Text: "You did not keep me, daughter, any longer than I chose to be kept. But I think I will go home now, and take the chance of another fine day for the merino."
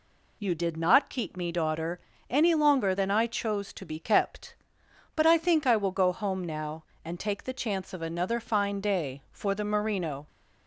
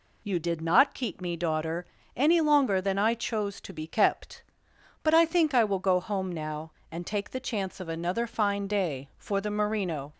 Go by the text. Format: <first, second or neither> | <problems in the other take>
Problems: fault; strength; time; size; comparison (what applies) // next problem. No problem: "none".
neither | none